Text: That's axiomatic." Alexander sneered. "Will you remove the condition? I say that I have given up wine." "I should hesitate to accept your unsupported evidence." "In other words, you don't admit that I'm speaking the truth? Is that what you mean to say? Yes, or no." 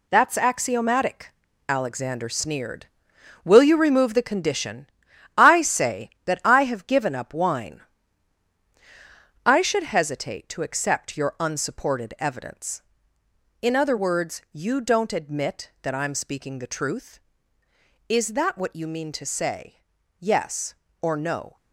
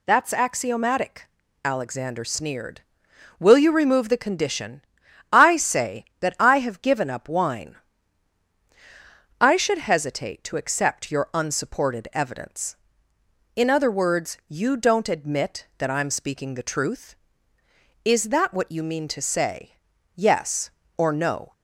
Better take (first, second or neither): second